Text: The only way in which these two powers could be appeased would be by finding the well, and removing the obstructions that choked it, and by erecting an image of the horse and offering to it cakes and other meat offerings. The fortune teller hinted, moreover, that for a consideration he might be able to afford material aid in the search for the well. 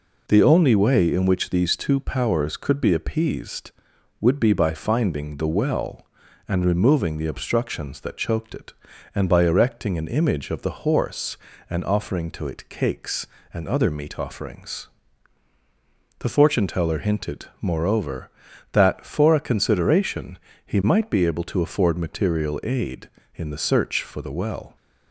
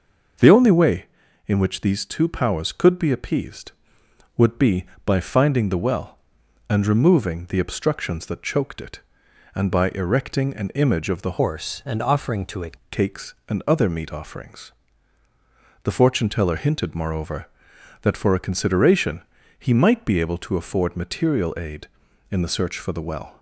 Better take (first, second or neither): first